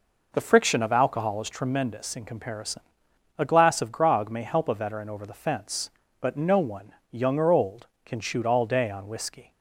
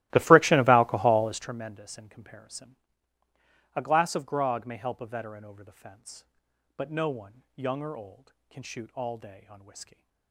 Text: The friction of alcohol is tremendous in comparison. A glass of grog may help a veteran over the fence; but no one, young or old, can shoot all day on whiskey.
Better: first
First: none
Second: starts louder than the rest; strong; until 1.6 s; 16.5 dB

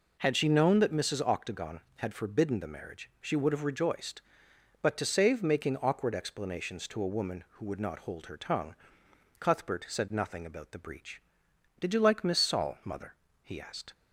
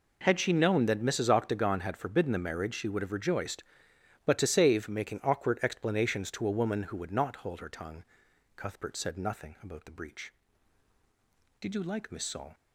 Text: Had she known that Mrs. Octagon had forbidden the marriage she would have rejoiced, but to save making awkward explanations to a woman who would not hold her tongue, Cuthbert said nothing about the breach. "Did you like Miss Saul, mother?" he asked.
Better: first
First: none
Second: stops before "mother he asked"; at 12.5 s

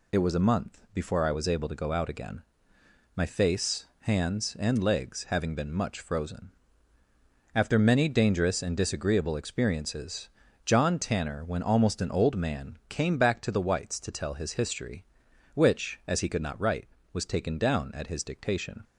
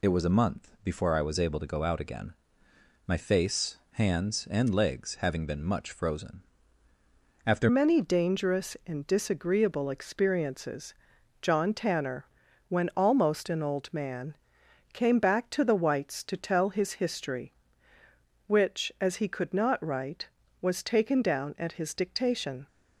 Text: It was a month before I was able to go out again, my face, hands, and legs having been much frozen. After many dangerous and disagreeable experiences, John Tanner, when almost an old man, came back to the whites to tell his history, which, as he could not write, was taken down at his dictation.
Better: first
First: none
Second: changes voice at "many"; from 7.6 s on; 15.0 s long

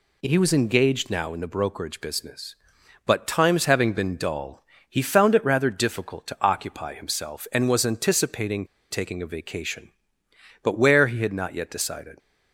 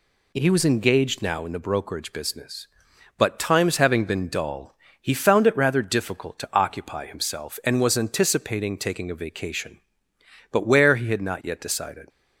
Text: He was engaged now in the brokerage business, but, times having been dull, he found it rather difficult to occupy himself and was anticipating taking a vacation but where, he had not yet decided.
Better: second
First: pauses between "anticipating" and "taking"; slight; at 8.6 s; 0.25 s long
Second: none

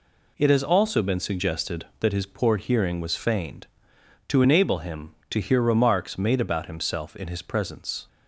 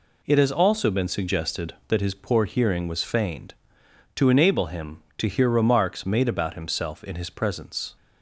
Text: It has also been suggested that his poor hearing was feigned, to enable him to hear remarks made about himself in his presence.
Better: neither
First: none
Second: none

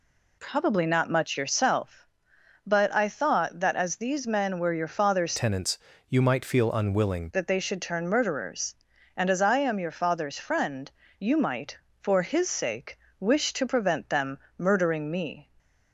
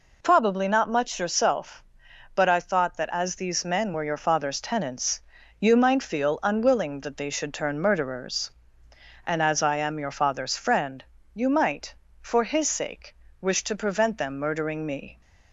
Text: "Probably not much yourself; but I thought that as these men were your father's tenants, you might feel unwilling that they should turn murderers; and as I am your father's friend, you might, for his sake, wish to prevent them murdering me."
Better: second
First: changes voice from "tenants" to "unwilling"; from 5.3 to 7.3 s; 2.0 s long // pauses between "them" and "murdering"; slight; at 14.3 s; 0.18 s long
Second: none

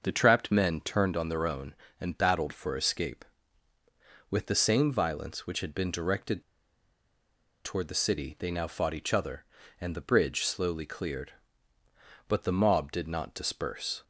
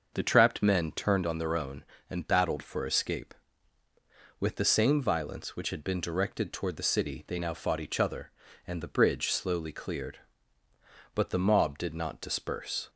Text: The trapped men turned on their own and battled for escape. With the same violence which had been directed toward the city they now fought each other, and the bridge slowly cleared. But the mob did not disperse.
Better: second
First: starts louder than the rest; until 1.0 s; 6 dB // pauses between "directed" and "toward"; at 6.4 s; 1.2 s long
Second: starts louder than the rest; until 1.1 s; 6 dB

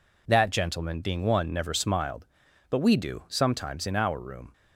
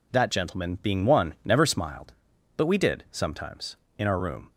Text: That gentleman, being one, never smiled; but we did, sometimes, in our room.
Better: second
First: says "do" for "did"; at 2.9 s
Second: none

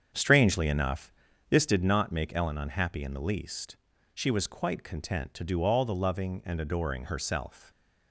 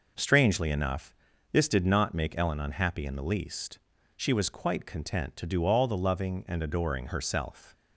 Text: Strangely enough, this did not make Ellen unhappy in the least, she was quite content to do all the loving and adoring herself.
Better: second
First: starts louder than the rest; strong; until 1.8 s; 7.5 dB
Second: none

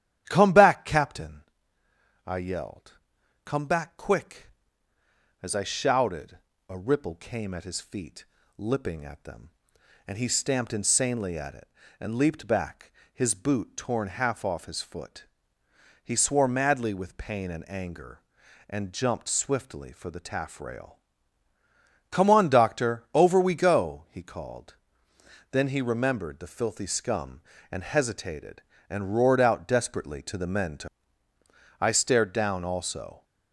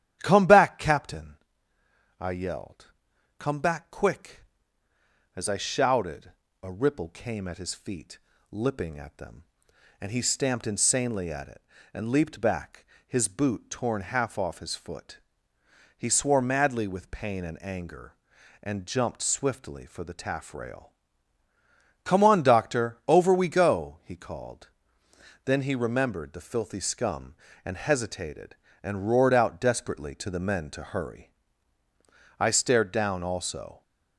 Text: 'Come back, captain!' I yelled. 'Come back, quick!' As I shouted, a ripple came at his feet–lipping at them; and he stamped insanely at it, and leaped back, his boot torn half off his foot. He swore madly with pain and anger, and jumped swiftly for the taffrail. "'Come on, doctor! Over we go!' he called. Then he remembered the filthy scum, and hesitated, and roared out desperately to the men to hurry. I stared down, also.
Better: second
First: starts louder than the rest; strong; until 1.2 s; 11.5 dB // skips "hurry"; at 31.3 s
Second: starts louder than the rest; strong; until 1.2 s; 11.5 dB

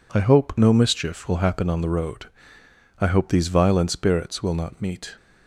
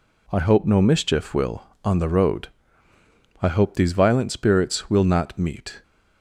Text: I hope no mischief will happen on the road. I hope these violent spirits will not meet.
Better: first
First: none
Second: skips "happen"; at 1.7 s

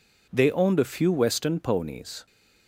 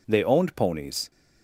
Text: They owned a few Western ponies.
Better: first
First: none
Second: skips "a few Western"; at 0.5 s

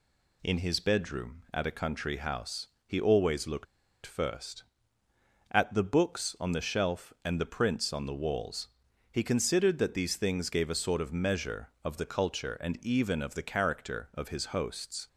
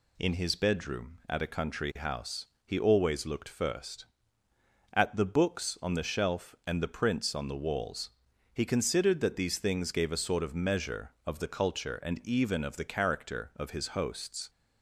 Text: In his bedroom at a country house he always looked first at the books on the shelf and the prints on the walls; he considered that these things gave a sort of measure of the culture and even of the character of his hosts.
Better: second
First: pauses between "house" and "he"; slight; at 2.6 s; 0.18 s long // pauses between "looked" and "first"; at 3.6 s; 0.39 s long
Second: pauses between "house" and "he"; slight; at 2.4 s; 0.18 s long

